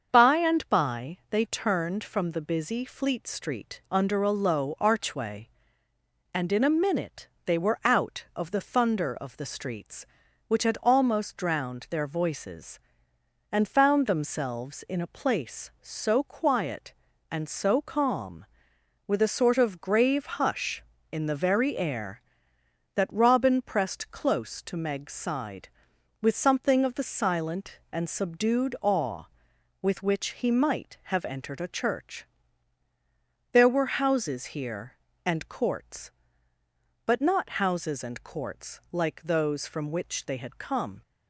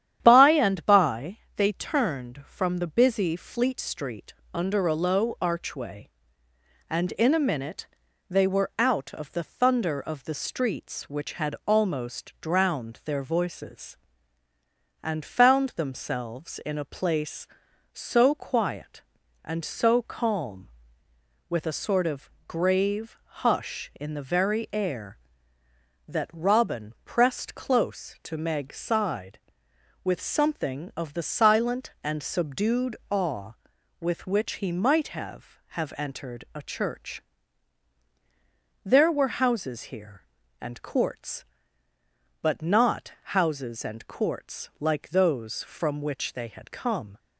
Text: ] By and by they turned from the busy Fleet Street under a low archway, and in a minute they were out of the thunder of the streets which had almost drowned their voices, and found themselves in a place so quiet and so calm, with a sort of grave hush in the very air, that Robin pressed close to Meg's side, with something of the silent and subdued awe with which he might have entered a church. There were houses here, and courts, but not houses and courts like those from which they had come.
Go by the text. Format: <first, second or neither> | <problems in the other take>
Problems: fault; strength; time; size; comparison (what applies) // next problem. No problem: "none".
first | starts louder than the rest; strong; until 1.2 s; 10.5 dB; also in the first // pauses between "by" and "they"; slight; at 1.3 s; 0.18 s long // pauses between "Street" and "under"; slight; at 4.3 s; 0.18 s long // pauses between "minute" and "they"; at 7.8 s; 0.42 s long; slight in the first // pauses between "of" and "grave"; slight; at 22.2 s; 0.18 s long // says "have" twice; at 35.6 s